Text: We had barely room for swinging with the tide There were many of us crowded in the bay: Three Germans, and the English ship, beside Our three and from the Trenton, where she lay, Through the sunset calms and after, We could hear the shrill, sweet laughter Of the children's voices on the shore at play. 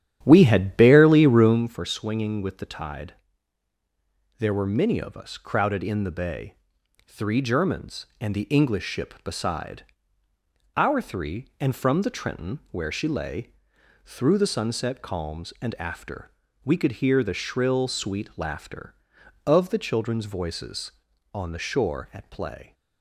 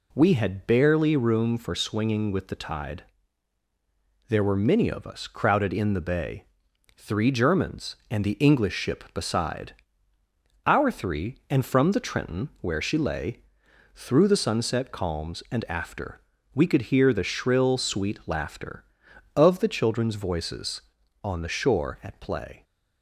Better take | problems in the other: second | starts louder than the rest; strong; until 1.6 s; 10.5 dB // pauses between "tide" and "There"; strong; at 3.1 s; 1.2 s long; strong in the second // pauses between "beside" and "Our"; noticeable; at 9.8 s; 0.90 s long; noticeable in the second

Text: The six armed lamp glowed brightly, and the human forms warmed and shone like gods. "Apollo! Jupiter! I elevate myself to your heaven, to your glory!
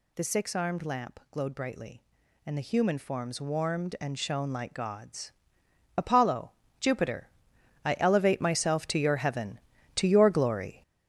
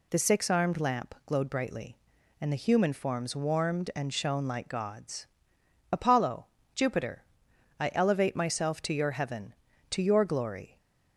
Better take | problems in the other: second | gets louder; strong; throughout; 8 dB

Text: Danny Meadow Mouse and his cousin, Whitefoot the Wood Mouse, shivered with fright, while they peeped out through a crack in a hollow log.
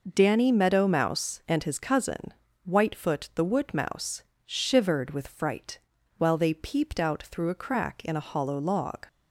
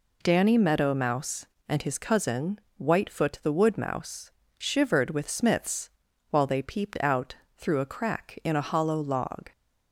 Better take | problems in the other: first | says "smiths" for "fright"; at 5.2 s // pauses between "out" and "through"; slight; at 7.3 s; 0.24 s long

